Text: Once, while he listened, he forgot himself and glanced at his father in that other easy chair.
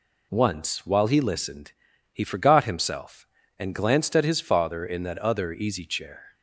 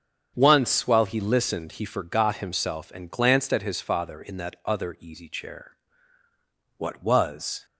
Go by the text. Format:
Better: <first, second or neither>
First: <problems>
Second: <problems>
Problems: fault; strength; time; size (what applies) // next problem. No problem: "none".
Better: first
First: none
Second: starts louder than the rest; strong; until 1.3 s; 7.5 dB // goes on to say "What was"; noticeable; from 6.7 s on; 0.88 s long